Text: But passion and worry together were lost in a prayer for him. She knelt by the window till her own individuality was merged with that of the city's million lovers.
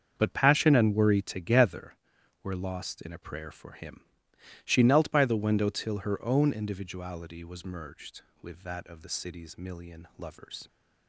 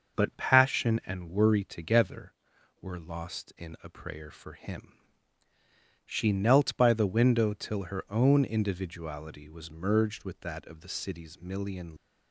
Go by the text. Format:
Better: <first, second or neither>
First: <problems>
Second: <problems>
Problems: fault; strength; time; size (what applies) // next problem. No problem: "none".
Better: first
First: starts louder than the rest; until 1.1 s; 7 dB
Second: starts louder than the rest; until 1.2 s; 6 dB // stops before "lovers"; at 11.9 s